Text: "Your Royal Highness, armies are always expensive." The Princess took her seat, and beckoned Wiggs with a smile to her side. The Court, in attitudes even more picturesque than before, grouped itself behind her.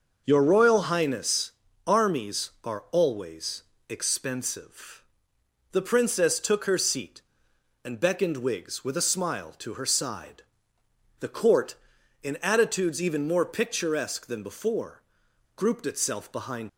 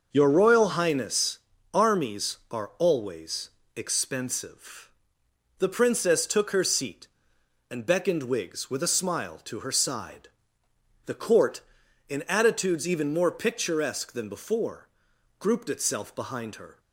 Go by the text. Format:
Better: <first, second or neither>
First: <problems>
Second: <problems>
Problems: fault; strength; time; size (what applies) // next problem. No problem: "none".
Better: second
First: pauses between "always" and "expensive"; slight; at 3.6 s; 0.26 s long // stops before "her"; at 16.6 s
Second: pauses between "always" and "expensive"; slight; at 3.5 s; 0.26 s long